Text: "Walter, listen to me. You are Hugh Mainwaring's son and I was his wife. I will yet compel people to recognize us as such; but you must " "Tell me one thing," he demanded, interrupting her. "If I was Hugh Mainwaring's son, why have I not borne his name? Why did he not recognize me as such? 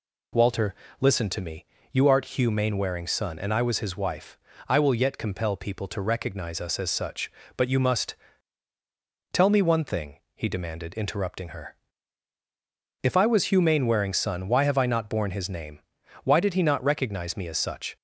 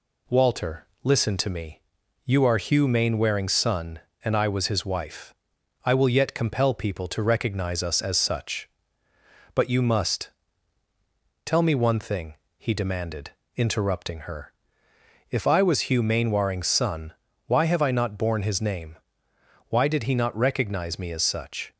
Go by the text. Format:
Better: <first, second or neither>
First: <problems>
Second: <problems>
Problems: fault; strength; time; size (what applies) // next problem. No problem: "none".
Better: second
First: says "art" for "are"; at 2.0 s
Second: none